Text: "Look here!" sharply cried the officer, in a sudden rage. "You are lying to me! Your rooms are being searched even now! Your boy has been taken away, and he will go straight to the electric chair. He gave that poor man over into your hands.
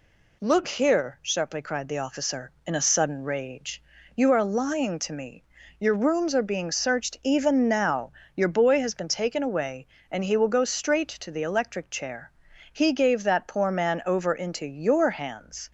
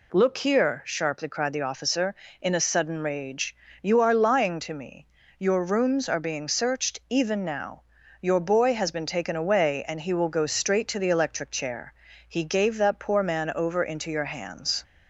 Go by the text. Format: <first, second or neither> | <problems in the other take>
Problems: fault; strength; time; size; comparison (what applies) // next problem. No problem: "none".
neither | none